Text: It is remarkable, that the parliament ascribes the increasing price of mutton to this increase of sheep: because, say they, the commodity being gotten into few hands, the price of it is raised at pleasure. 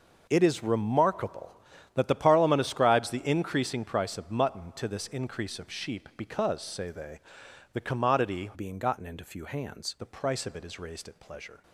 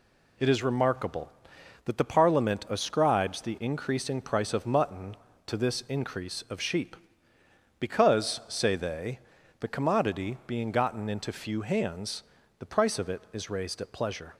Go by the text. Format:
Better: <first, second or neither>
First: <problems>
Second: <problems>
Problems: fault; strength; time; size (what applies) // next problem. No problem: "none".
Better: second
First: changes voice from "being" to "hands"; from 8.5 to 9.9 s; 1.4 s long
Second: none